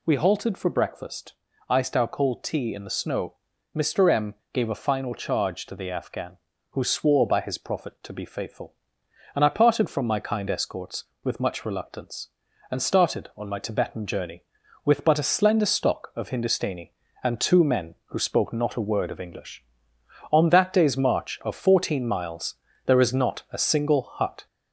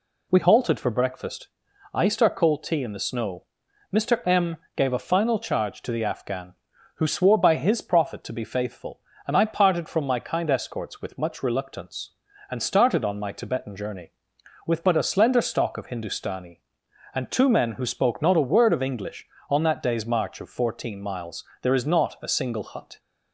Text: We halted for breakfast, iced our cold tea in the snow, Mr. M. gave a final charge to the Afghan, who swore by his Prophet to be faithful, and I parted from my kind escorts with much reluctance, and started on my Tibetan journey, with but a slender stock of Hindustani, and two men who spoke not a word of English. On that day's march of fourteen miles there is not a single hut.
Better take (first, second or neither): second